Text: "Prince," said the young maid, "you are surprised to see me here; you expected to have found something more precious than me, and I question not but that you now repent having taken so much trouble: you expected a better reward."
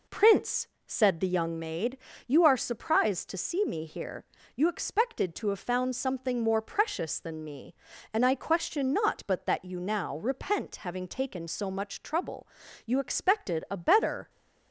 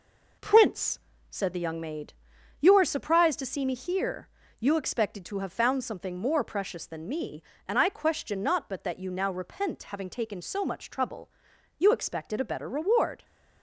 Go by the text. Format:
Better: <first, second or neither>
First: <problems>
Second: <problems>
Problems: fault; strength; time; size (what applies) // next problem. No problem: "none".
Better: second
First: stops before "reward"; at 14.2 s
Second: none